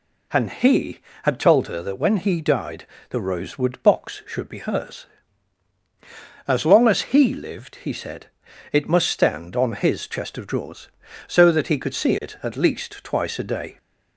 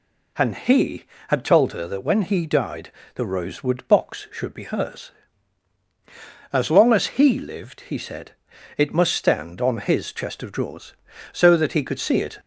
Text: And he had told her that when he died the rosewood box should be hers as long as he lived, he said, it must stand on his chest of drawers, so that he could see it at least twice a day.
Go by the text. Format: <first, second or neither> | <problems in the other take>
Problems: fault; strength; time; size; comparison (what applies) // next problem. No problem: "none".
first | pauses between "died" and "the"; slight; at 2.9 s; 0.24 s long; slight in the first // stops before "at least twice a day"; at 12.4 s